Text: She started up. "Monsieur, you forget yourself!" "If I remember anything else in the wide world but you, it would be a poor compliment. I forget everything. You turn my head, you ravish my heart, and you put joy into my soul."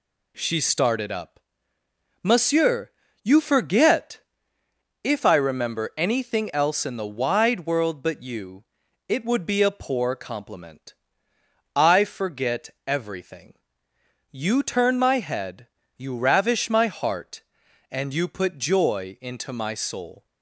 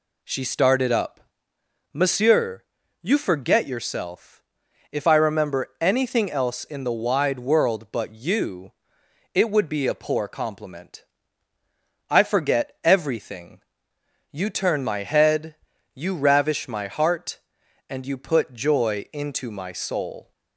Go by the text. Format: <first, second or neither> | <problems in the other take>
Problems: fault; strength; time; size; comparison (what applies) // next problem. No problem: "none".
second | skips "yourself"; at 4.6 s